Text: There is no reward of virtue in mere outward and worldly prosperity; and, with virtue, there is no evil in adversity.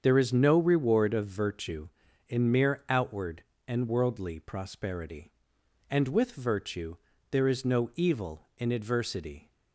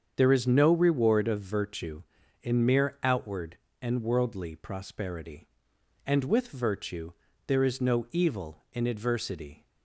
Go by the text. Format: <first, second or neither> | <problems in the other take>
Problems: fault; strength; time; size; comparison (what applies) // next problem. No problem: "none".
neither | starts louder than the rest; strong; the same in both